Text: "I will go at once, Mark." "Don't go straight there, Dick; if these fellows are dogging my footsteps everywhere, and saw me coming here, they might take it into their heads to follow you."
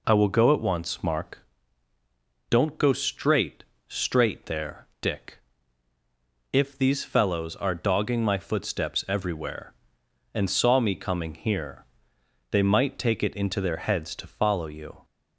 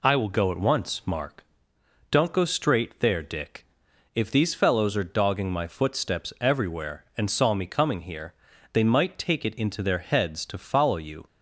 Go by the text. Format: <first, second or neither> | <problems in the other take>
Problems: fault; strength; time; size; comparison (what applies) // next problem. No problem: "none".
second | says "straight" twice; at 3.8 s